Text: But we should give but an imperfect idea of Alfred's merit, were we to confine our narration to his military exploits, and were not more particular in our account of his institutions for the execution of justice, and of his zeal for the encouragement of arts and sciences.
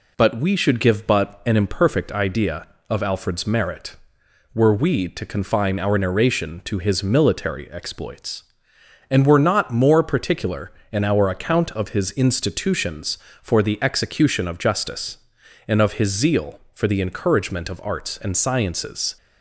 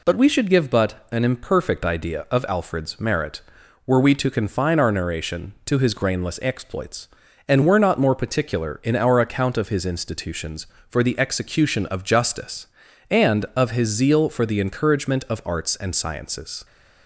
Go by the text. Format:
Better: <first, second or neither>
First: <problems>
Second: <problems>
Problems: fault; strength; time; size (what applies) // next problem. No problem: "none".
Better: first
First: none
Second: says "grainless" for "military"; at 5.9 s